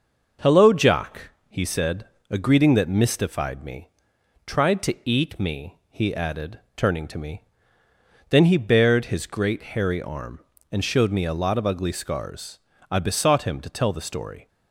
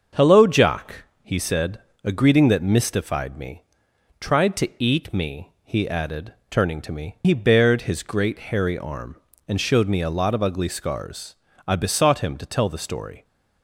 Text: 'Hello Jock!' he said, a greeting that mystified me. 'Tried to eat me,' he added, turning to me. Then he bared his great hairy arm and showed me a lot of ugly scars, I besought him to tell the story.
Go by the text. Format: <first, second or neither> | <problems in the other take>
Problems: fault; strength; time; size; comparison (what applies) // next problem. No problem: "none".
first | starts louder than the rest; until 1.3 s; 6.5 dB // skips "Then"; at 7.2 s